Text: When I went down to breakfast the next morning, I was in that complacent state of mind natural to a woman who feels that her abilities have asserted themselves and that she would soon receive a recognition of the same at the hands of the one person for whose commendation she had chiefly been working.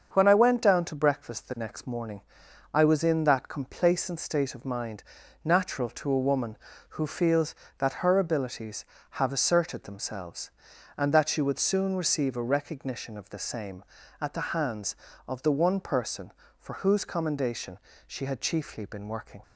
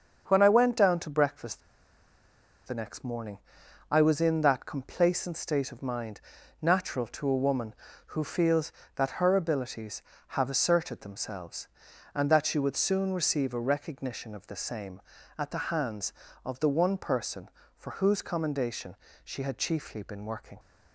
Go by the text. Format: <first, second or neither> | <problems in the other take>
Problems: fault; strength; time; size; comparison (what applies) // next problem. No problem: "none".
first | starts louder than the rest; until 1.3 s; 7 dB; also in the first // pauses between "breakfast" and "the"; at 1.6 s; 1.0 s long // pauses between "mind" and "natural"; at 6.1 s; 0.42 s long; also in the first // pauses between "commendation" and "she"; slight; at 18.9 s; 0.26 s long; slight in the first